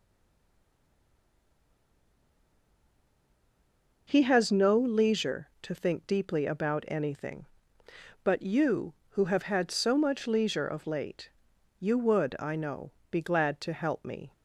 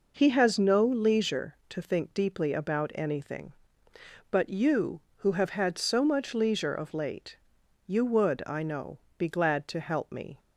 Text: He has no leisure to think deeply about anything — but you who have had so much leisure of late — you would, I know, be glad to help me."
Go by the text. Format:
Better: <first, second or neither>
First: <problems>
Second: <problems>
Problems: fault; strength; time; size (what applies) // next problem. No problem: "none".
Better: second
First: stays silent before the first word; strong; until 4.0 s; 4.0 s long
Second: none